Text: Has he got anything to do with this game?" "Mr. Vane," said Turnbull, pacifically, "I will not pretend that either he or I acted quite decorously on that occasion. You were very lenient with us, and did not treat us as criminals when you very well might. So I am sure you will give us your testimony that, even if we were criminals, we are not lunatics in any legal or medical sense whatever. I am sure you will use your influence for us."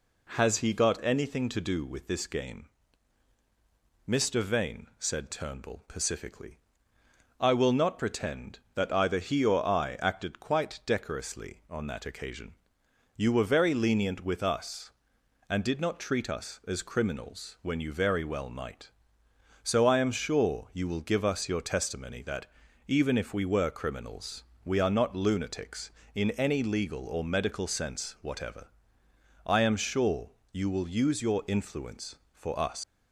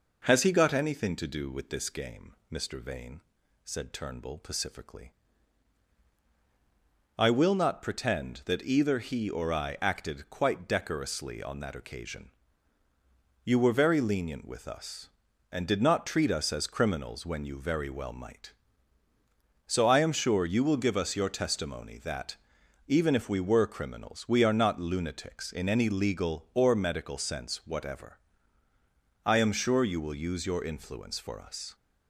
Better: second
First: pauses between "sure" and "you"; slight; at 30.3 s; 0.20 s long // leaves "us" unfinished; at 32.8 s; 140 ms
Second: none

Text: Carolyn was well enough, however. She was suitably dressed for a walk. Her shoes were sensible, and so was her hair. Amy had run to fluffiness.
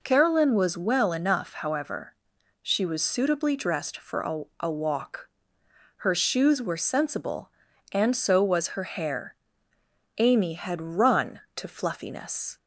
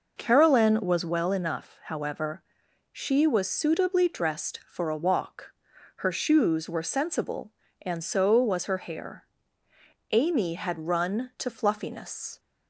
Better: second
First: says "a" twice; at 4.5 s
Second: none

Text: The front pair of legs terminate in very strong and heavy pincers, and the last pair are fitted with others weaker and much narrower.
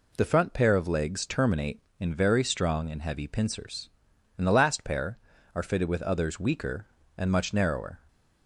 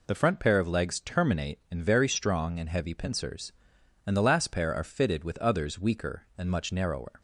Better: neither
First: none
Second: none

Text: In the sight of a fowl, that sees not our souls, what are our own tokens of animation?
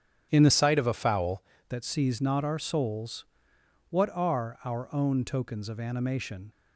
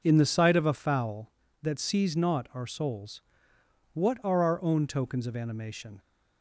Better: second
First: starts louder than the rest; strong; until 1.3 s; 9 dB // changes voice from "sight" to "fowl"; from 0.5 to 1.4 s; 0.9 s long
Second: none

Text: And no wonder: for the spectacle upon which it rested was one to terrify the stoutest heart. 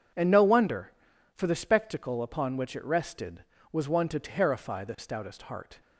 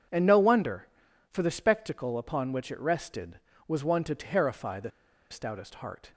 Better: first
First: none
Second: pauses between "the" and "stoutest"; at 4.9 s; 0.42 s long

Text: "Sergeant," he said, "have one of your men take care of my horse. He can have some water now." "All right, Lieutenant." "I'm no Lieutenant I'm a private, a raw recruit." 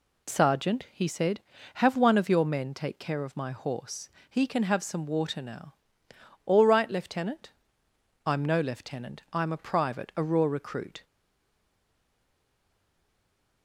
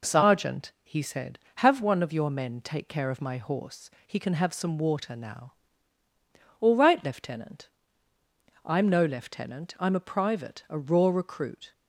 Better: second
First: stays silent after the last word; strong; from 11.0 s on; 2.6 s long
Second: none

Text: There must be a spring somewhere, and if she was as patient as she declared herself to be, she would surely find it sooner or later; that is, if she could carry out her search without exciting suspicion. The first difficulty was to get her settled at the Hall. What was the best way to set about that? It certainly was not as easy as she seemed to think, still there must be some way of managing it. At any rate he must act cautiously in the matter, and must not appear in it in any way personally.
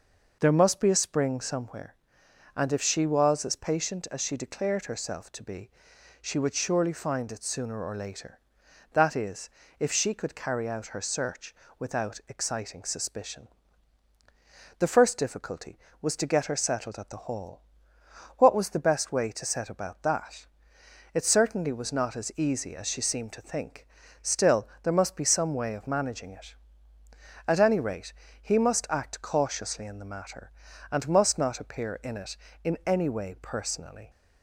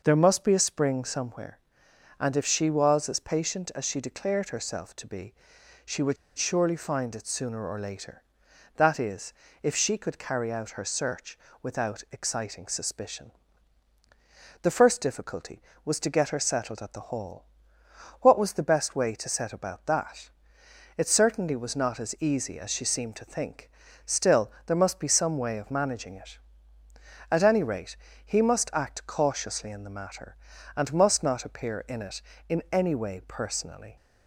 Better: first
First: pauses between "search" and "without"; slight; at 11.5 s; 0.24 s long // pauses between "still" and "there"; slight; at 24.6 s; 0.16 s long // pauses between "rate" and "he"; slight; at 28.1 s; 0.28 s long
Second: pauses between "would" and "surely"; slight; at 6.1 s; 0.21 s long // pauses between "search" and "without"; slight; at 11.3 s; 0.24 s long // pauses between "still" and "there"; slight; at 24.4 s; 0.16 s long // pauses between "rate" and "he"; slight; at 27.9 s; 0.28 s long

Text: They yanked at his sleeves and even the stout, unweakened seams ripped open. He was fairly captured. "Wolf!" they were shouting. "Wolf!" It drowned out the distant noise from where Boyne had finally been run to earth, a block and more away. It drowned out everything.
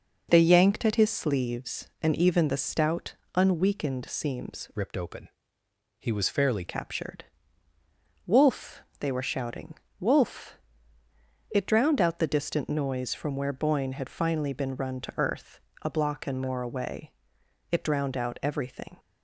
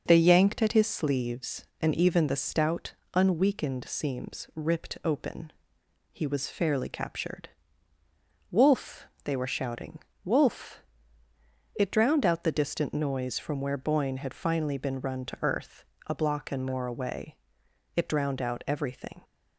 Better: second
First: changes voice from "ripped" to "fairly"; from 4.7 to 6.6 s; 1.9 s long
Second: none

